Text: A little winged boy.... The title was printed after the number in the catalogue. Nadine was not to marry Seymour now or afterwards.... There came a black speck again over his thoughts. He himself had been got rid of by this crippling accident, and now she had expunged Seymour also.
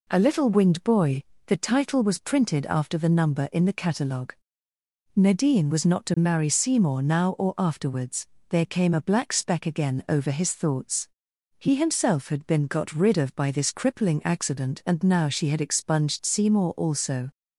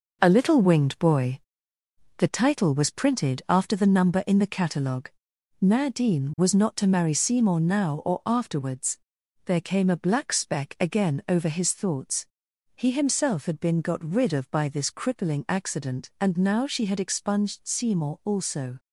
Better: first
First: none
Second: gets quieter; strong; throughout; 7 dB

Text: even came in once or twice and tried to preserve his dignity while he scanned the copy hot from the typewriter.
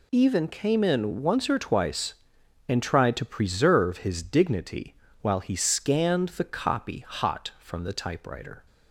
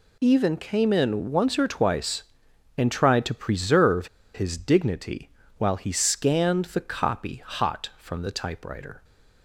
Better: first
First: pauses between "dignity" and "while"; slight; at 4.9 s; 0.26 s long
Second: pauses between "preserve" and "his"; slight; at 4.0 s; 0.26 s long // pauses between "dignity" and "while"; slight; at 5.2 s; 0.28 s long

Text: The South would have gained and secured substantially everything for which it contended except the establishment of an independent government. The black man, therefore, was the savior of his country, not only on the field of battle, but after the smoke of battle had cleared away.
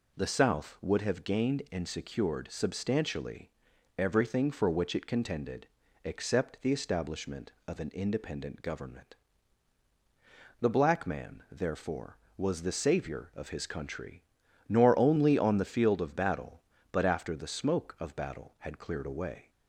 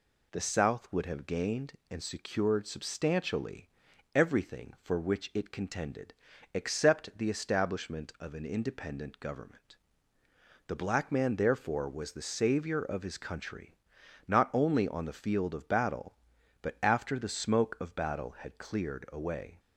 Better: second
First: pauses between "substantially" and "everything"; noticeable; at 3.4 s; 0.48 s long // pauses between "contended" and "except"; at 5.6 s; 0.38 s long // says "nor" for "not"; at 14.6 s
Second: pauses between "substantially" and "everything"; noticeable; at 3.6 s; 0.46 s long // pauses between "contended" and "except"; at 6.1 s; 0.40 s long

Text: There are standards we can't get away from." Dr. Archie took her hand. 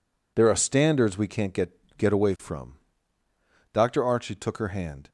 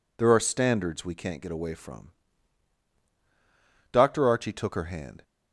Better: second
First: says "get" twice; at 1.9 s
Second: none

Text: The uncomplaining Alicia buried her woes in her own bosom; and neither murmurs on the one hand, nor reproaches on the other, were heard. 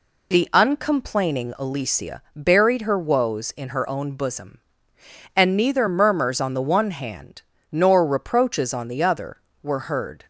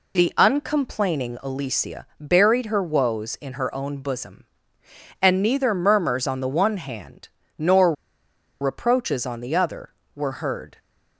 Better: first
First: none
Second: pauses between "nor" and "reproaches"; noticeable; at 7.9 s; 0.68 s long

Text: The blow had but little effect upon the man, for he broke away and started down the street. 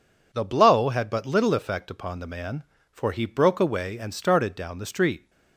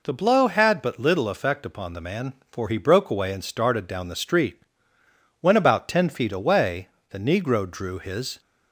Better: first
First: none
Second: goes on to say "When about ten feet away the Negro drew his"; strong; from 5.4 s on; 3.0 s long

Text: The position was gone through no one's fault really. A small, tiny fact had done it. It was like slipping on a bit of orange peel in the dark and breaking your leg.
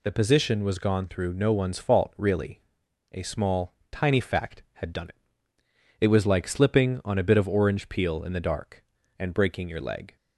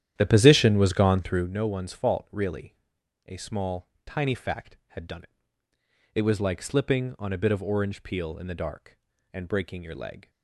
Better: first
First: none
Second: starts louder than the rest; strong; until 1.6 s; 11 dB

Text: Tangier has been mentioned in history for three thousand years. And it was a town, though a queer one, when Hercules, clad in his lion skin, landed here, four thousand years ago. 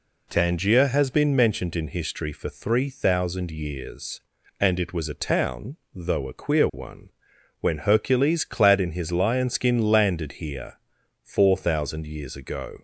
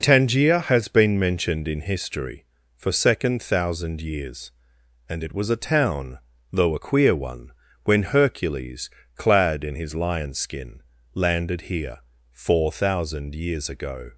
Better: first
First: none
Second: says "second" for "three"; at 2.9 s

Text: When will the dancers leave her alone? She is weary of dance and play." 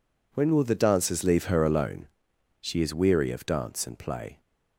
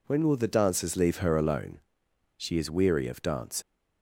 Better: first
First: none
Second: stops before "and play"; at 3.6 s

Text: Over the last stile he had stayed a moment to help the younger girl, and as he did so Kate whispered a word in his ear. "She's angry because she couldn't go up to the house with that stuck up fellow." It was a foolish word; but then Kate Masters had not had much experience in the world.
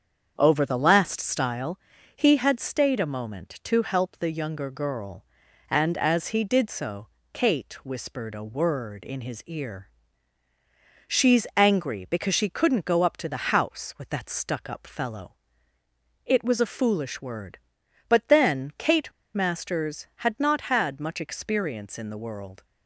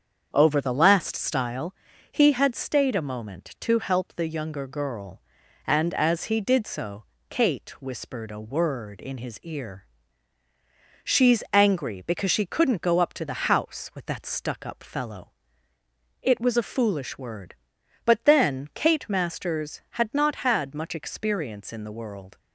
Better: second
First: starts louder than the rest; strong; until 1.3 s; 7.5 dB // pauses between "stile" and "he"; at 1.7 s; 0.38 s long // pauses between "so" and "Kate"; slight; at 7.0 s; 0.24 s long // pauses between "Kate" and "Masters"; slight; at 19.1 s; 0.24 s long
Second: starts louder than the rest; strong; until 1.3 s; 7.5 dB // pauses between "stile" and "he"; at 1.7 s; 0.38 s long // pauses between "so" and "Kate"; slight; at 7.0 s; 0.24 s long

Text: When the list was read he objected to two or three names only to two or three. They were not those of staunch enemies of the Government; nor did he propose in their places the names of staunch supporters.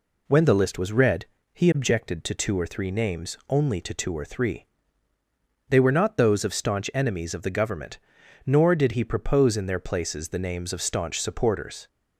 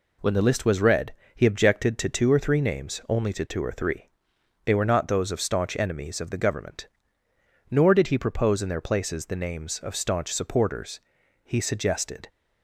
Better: first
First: pauses between "read" and "he"; slight; at 1.2 s; 0.28 s long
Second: pauses between "read" and "he"; slight; at 1.1 s; 0.20 s long // goes on to say "He suggested"; noticeable; from 11.4 s on; 0.86 s long

